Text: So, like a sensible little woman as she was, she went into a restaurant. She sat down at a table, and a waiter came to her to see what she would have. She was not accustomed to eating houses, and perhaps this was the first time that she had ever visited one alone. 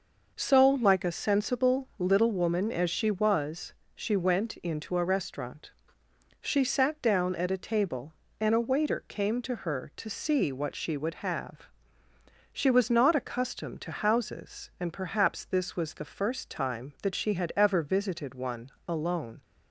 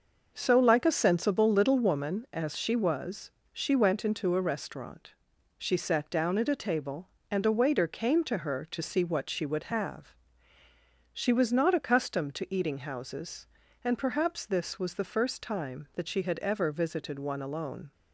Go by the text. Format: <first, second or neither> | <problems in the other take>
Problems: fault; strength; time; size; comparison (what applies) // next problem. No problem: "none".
second | skips "eating"; at 13.9 s // pauses between "one" and "alone"; slight; at 18.7 s; 0.16 s long